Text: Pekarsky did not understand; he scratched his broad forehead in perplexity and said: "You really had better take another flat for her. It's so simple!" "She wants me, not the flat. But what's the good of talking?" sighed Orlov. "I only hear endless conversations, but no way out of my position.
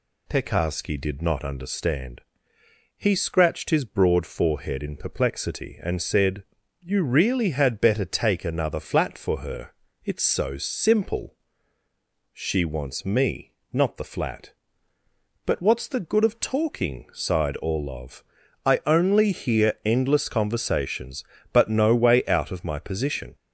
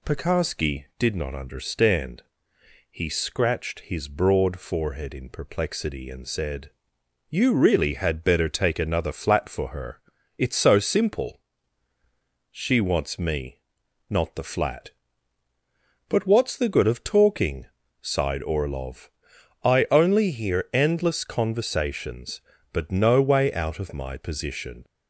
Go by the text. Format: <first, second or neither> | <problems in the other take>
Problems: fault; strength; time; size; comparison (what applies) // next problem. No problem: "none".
neither | none